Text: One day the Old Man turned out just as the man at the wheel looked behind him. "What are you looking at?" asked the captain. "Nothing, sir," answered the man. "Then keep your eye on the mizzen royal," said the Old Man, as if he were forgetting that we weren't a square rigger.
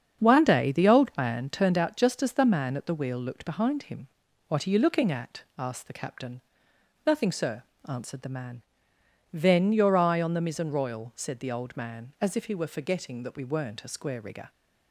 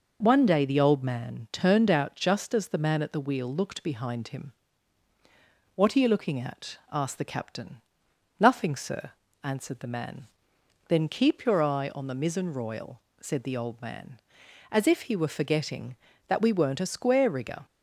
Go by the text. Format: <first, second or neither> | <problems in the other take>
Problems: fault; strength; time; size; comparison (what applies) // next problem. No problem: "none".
second | starts louder than the rest; strong; until 1.2 s; 7.5 dB // skips "keep"; at 9.7 s